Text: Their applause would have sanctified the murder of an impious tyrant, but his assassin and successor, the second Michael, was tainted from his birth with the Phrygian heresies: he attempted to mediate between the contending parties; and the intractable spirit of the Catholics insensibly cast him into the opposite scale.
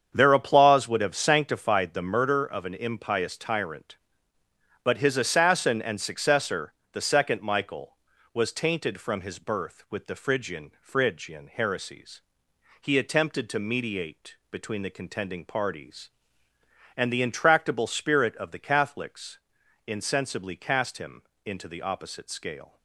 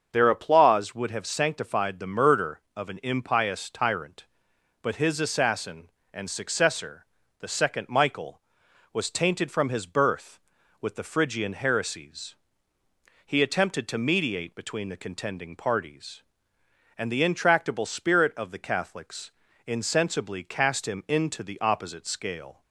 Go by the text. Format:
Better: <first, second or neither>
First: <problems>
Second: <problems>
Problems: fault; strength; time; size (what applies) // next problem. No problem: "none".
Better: second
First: starts louder than the rest; strong; until 1.1 s; 7.5 dB // says "Phrygian" twice; at 10.8 s // pauses between "mediate" and "between"; slight; at 14.3 s; 0.16 s long // pauses between "Catholics" and "insensibly"; noticeable; at 19.3 s; 0.48 s long // pauses between "him" and "into"; slight; at 21.2 s; 0.20 s long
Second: starts louder than the rest; until 1.1 s; 6.5 dB // pauses between "Catholics" and "insensibly"; slight; at 19.3 s; 0.36 s long